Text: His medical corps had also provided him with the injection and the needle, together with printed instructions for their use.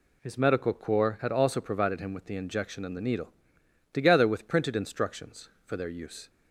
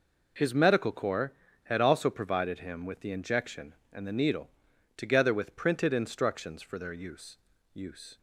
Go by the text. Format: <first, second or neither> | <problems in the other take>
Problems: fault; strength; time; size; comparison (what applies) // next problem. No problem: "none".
first | says "use" twice; at 7.7 s